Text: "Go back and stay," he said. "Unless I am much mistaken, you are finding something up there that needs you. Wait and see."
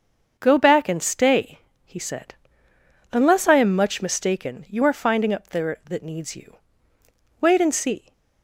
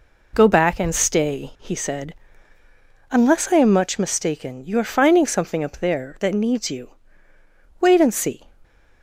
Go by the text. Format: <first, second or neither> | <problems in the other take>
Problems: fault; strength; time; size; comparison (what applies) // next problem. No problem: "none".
second | starts louder than the rest; until 1.4 s; 7 dB // skips "something"; at 5.3 s